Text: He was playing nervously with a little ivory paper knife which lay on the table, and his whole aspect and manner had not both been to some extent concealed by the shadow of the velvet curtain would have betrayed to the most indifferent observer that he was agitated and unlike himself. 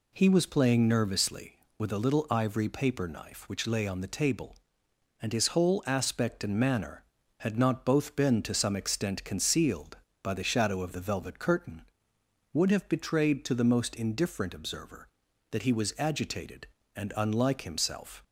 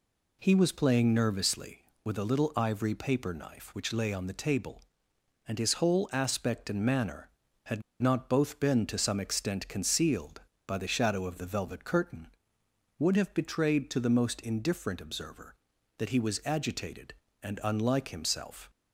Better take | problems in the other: first | pauses between "had" and "not"; slight; at 7.8 s; 0.19 s long

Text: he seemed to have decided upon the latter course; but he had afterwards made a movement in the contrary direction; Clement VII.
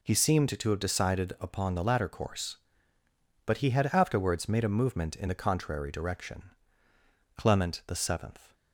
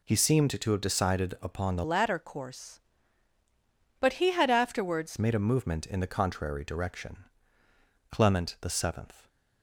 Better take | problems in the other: first | changes voice from "latter" to "afterwards"; from 1.8 to 5.1 s; 3.3 s long

